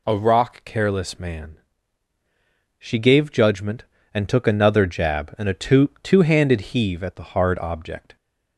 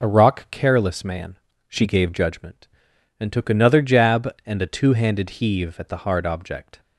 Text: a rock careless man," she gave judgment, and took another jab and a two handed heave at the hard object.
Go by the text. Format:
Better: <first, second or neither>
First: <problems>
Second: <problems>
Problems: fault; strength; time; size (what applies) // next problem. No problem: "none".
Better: second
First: says "two" twice; at 6.0 s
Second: none